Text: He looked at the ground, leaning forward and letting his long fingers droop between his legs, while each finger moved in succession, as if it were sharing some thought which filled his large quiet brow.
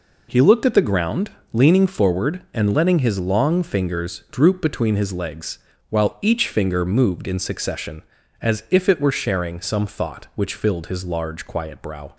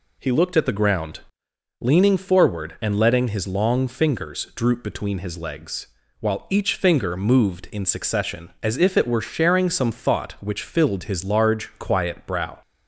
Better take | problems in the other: neither | none

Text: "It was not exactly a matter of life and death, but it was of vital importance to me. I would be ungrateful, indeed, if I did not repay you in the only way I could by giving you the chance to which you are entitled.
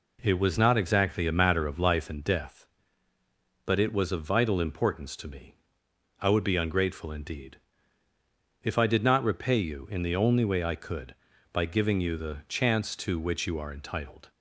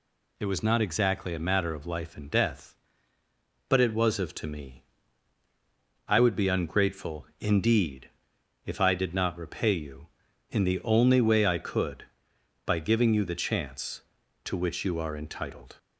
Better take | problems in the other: first | skips "vital importance"; at 4.3 s

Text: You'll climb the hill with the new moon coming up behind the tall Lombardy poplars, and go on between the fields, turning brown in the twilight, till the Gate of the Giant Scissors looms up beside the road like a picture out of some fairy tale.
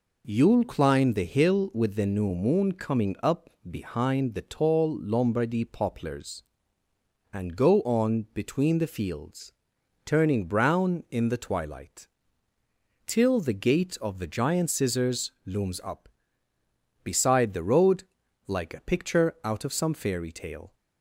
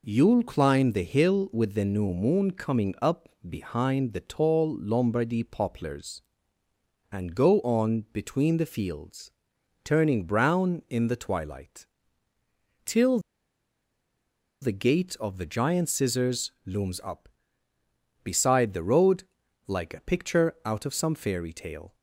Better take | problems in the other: first | pauses between "up" and "behind"; slight; at 3.2 s; 0.22 s long; slight in the first // pauses between "till" and "the"; strong; at 13.1 s; 1.4 s long // pauses between "road" and "like"; at 19.2 s; 0.42 s long; also in the first

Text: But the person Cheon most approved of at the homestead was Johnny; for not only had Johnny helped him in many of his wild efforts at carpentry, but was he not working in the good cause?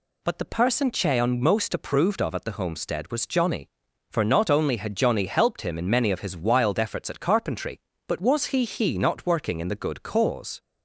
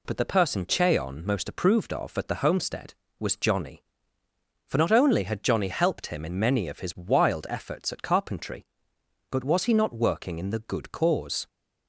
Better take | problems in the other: second | says "he" twice; at 8.6 s

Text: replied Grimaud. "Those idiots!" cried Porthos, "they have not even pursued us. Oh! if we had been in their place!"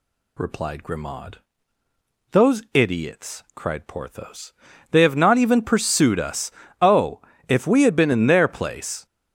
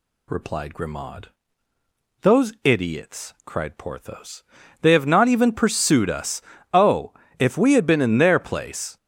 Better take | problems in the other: neither | none

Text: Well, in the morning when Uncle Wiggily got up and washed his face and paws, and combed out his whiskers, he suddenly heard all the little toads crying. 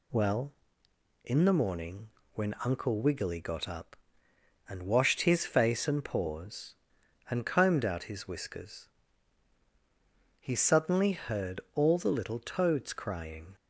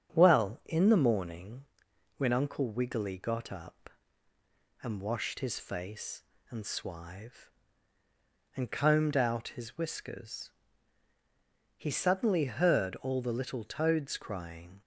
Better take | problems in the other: first | starts louder than the rest; strong; until 1.1 s; 8 dB // pauses between "morning" and "when"; noticeable; at 1.6 s; 0.54 s long; slight in the first // says "swive" for "paws"; at 6.6 s

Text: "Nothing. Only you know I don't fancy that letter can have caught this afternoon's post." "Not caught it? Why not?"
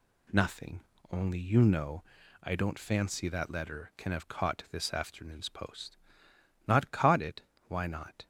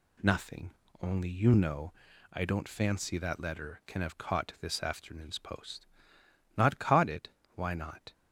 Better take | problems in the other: neither | pauses between "know" and "I"; the same in both

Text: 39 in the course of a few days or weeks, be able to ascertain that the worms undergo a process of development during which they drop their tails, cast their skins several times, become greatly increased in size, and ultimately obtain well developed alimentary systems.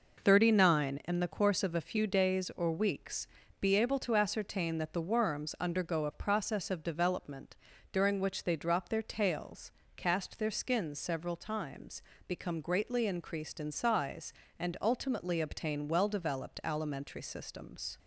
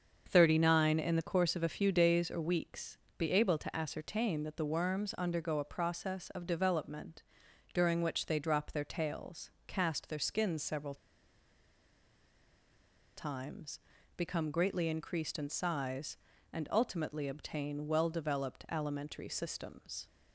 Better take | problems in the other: first | starts louder than the rest; until 1.2 s; 6.5 dB // pauses between "development" and "during"; noticeable; at 7.2 s; 0.50 s long; slight in the first // pauses between "several" and "times"; strong; at 10.9 s; 2.2 s long

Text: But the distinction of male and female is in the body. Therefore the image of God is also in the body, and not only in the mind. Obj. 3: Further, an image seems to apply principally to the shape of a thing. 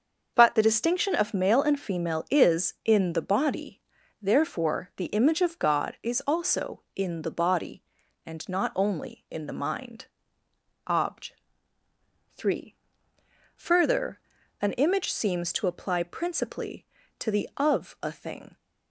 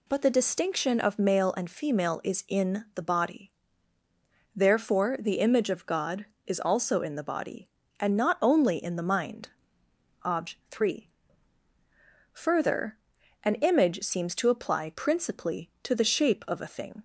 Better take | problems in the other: second | starts louder than the rest; until 1.3 s; 6 dB // skips "shape"; at 17.5 s

